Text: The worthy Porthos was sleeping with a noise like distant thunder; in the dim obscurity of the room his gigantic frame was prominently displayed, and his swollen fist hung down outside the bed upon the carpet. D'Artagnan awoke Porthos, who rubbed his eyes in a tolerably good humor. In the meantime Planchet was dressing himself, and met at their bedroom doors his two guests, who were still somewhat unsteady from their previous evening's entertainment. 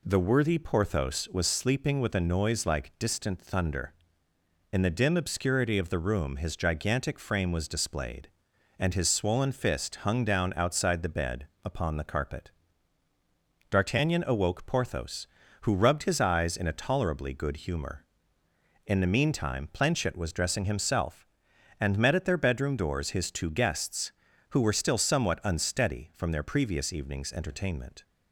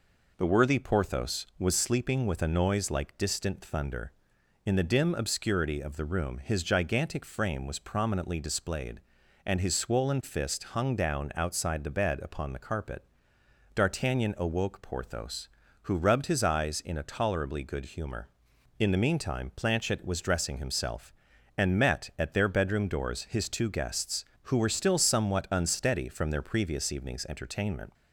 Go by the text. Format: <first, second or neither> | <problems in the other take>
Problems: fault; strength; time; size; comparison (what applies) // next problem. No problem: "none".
second | skips "prominently"; at 7.7 s // pauses between "bed" and "upon"; slight; at 11.4 s; 0.18 s long